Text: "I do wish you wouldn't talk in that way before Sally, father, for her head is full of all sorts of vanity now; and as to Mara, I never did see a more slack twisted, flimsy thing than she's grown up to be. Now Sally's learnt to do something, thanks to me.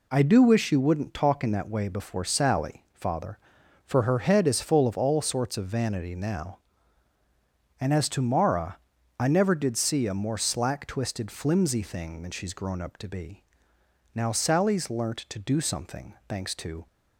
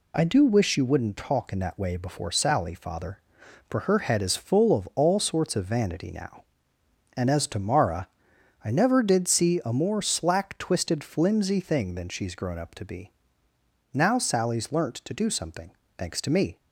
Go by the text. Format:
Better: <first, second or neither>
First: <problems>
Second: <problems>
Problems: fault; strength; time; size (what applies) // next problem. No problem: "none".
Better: second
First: stops before "me"; at 16.8 s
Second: none